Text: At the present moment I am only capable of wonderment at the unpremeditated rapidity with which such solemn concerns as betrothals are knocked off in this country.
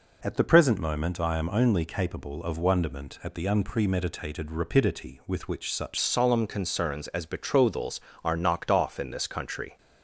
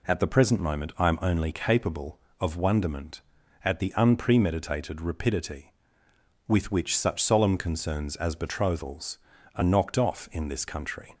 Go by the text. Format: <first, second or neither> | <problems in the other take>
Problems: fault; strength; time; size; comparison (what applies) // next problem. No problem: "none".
second | changes voice at "solemn"; from 5.9 s on; 3.8 s long